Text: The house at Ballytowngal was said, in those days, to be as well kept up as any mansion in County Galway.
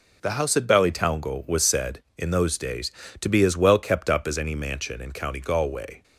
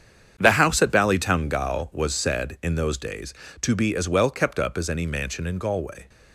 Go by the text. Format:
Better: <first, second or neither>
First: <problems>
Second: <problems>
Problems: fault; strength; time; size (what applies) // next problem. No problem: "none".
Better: first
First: none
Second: starts louder than the rest; strong; until 1.3 s; 8 dB // skips "County"; at 5.5 s